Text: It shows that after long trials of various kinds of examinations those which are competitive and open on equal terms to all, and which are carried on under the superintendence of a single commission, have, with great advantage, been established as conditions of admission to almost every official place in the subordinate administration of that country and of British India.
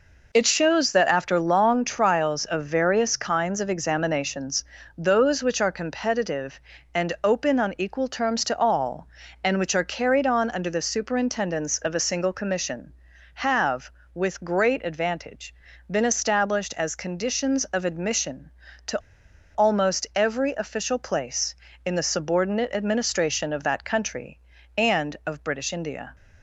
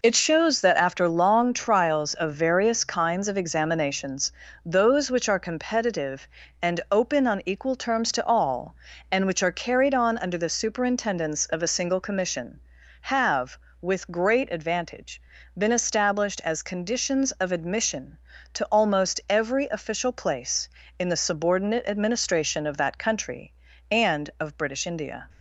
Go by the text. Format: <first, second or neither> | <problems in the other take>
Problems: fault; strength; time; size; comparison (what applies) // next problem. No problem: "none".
second | pauses between "examinations" and "those"; slight; at 4.6 s; 0.32 s long; slight in the second // pauses between "to" and "almost"; noticeable; at 18.9 s; 0.56 s long